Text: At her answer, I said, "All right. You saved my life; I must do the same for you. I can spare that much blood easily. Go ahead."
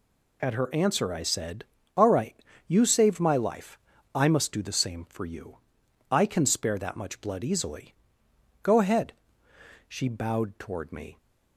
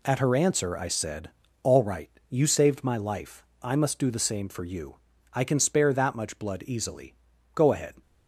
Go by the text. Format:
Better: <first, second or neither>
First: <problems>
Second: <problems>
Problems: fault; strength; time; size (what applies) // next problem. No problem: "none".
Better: second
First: goes on to say "She bowed toward me"; noticeable; from 9.8 s on; 1.3 s long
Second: none